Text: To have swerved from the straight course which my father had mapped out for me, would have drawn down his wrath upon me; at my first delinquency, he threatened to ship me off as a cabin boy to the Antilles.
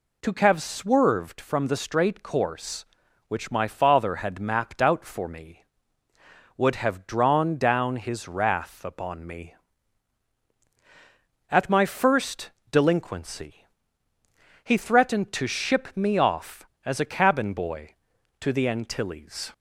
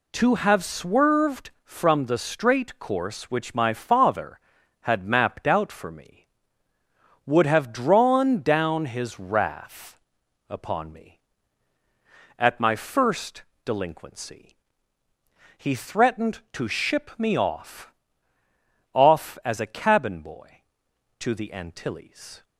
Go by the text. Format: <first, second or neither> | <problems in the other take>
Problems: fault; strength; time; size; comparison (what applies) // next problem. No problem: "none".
first | pauses between "wrath" and "upon"; noticeable; at 9.9 s; 0.50 s long // pauses between "first" and "delinquency"; slight; at 13.4 s; 0.24 s long; slight in the first // says "off" twice; at 18.9 s